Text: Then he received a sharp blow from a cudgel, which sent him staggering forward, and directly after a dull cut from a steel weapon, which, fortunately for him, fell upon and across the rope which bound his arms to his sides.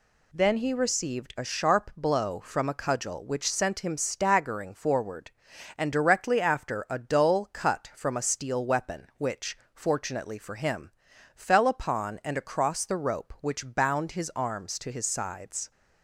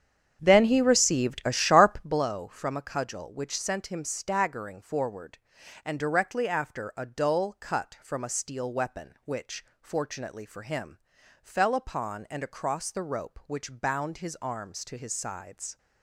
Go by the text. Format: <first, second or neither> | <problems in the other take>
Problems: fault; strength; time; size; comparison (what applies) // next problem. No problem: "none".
first | starts louder than the rest; strong; until 2.3 s; 8 dB